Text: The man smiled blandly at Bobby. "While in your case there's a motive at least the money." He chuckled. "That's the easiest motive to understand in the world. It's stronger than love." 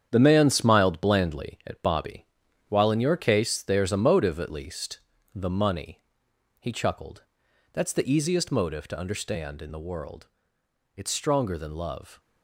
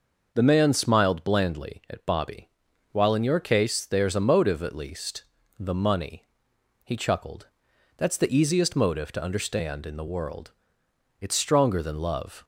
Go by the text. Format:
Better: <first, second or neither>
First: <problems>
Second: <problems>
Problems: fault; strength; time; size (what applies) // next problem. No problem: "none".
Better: second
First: gets quieter; strong; throughout; 8 dB // pauses between "least" and "the"; slight; at 4.9 s; 0.34 s long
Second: pauses between "least" and "the"; slight; at 5.2 s; 0.34 s long